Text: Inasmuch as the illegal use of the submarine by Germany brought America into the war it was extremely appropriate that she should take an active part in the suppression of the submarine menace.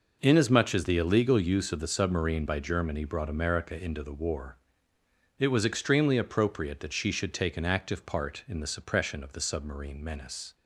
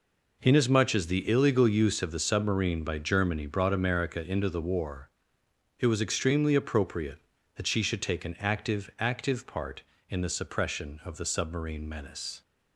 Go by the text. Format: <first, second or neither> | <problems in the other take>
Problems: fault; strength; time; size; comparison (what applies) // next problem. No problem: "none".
first | pauses between "war" and "it"; noticeable; at 5.0 s; 0.70 s long; noticeable in the first // says "active" twice; at 8.9 s